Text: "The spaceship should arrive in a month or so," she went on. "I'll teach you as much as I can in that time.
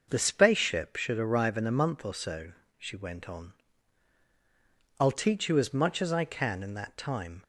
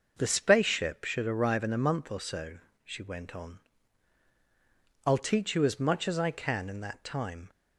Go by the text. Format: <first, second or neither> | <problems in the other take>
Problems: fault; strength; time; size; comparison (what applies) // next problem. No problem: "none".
neither | none